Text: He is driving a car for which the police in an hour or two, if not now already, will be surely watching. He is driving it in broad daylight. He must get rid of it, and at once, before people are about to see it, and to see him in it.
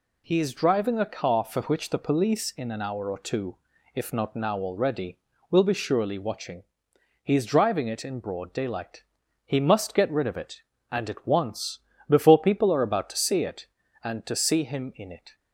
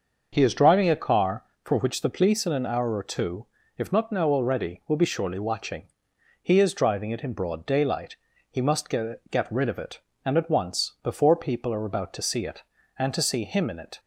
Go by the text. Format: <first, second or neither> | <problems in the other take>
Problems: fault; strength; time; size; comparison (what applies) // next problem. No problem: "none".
first | starts louder than the rest; until 1.3 s; 6 dB // says "get" twice; at 9.2 s